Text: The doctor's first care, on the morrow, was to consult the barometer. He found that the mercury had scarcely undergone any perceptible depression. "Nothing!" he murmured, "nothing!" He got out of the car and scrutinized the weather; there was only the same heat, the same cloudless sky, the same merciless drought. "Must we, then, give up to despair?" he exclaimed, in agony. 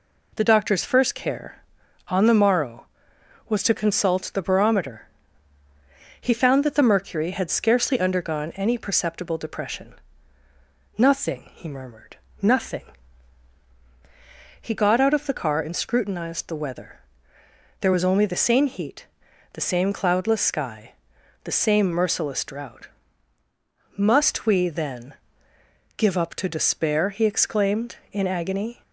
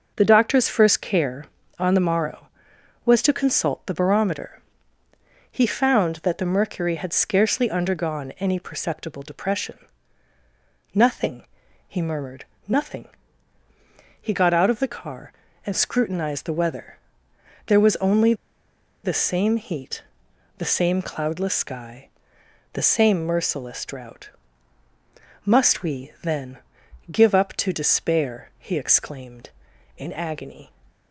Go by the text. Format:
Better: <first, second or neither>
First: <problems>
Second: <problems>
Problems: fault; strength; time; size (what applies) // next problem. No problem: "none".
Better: first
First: none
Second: pauses between "only" and "the"; noticeable; at 18.3 s; 0.70 s long